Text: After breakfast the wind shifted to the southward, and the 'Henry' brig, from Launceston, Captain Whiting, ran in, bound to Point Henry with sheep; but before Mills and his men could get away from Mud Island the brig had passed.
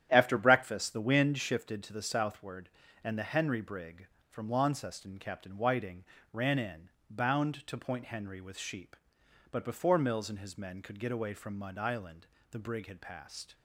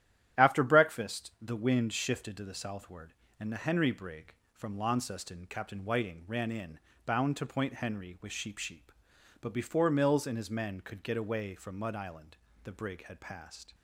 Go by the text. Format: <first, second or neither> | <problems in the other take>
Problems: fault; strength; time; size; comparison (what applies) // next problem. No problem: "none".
first | starts louder than the rest; strong; until 1.5 s; 11 dB; strong in the first // says "sheep" twice; at 8.5 s // pauses between "Island" and "the"; slight; at 12.3 s; 0.26 s long; slight in the first